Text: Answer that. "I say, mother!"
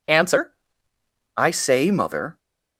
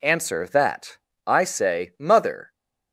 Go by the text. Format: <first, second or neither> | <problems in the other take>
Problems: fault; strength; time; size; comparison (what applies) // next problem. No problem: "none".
second | skips "that"; at 0.9 s